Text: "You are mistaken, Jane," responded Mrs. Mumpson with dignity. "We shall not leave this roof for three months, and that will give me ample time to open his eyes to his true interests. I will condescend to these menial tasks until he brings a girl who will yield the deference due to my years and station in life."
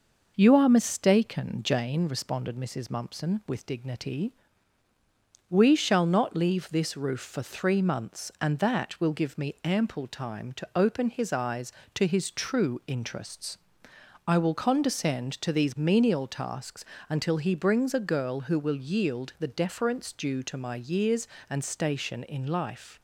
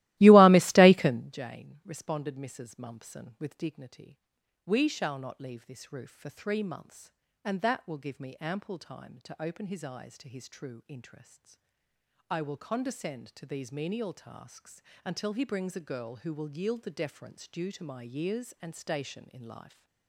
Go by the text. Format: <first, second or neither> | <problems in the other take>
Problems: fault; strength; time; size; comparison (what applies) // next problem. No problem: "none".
first | starts louder than the rest; strong; until 1.4 s; 17.5 dB // pauses between "tasks" and "until"; slight; at 14.8 s; 0.24 s long; slight in the first